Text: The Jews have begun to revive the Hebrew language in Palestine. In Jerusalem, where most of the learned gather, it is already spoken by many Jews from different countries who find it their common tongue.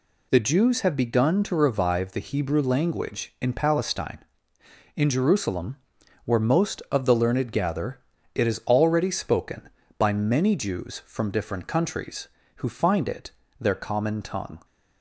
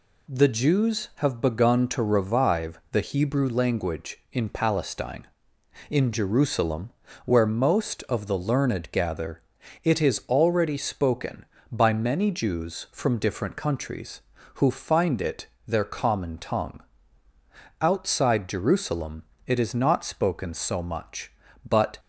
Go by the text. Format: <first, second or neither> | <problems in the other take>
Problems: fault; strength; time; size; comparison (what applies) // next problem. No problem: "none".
first | pauses between "it" and "their"; slight; at 15.4 s; 0.20 s long; slight in the first // goes on to say "Outside Jerusalem it is not spoken so much but"; strong; from 17.8 s on; 4.1 s long